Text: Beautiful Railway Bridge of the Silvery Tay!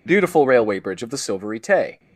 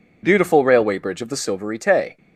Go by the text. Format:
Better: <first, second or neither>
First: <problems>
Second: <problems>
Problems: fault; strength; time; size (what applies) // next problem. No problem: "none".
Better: neither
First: none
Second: none